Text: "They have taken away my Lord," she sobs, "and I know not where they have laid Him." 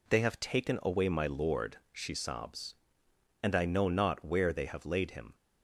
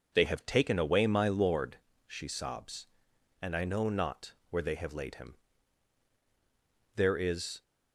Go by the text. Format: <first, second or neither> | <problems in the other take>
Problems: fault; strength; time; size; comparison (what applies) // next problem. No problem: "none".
first | pauses between "not" and "where"; slight; at 4.3 s; 0.16 s long // goes on to say "There is"; noticeable; from 6.9 s on; 0.66 s long